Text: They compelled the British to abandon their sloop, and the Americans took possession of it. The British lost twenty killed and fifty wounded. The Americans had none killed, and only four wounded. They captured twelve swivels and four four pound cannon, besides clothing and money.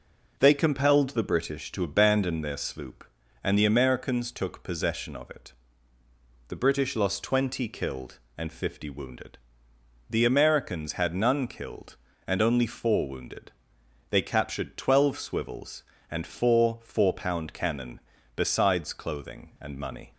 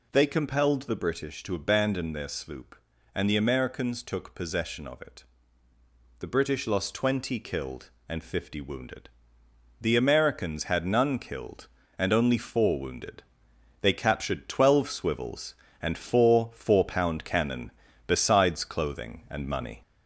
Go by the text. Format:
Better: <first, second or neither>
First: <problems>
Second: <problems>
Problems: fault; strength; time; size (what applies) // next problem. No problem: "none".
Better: first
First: none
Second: gets louder; slight; throughout; 2.5 dB